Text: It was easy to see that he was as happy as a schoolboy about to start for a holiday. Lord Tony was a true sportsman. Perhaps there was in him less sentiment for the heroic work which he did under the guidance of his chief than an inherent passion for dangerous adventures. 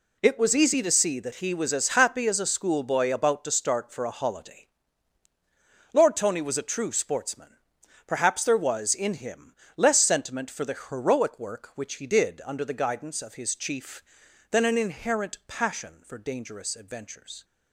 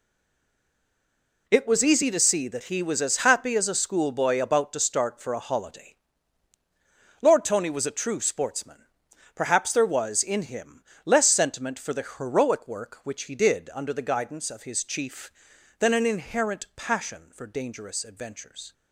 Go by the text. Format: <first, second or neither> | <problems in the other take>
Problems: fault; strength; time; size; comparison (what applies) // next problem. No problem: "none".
first | stays silent before the first word; noticeable; until 1.4 s; 1.4 s long // pauses between "him" and "less"; slight; at 10.8 s; 0.22 s long; slight in the first